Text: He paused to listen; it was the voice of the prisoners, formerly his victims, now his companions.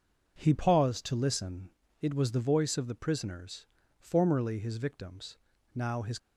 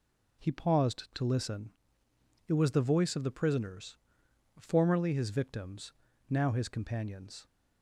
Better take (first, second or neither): second